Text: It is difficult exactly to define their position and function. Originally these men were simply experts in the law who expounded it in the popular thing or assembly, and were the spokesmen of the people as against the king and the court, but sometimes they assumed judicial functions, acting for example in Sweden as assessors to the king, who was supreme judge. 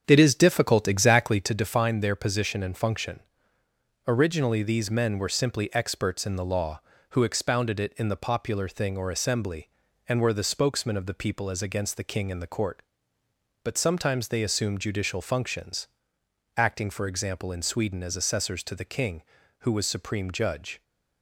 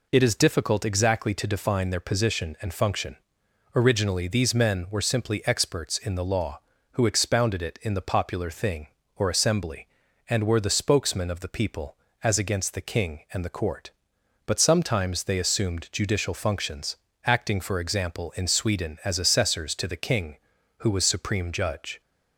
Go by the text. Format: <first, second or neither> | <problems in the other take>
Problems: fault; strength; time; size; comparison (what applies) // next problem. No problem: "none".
second | starts louder than the rest; strong; until 1.6 s; 7.5 dB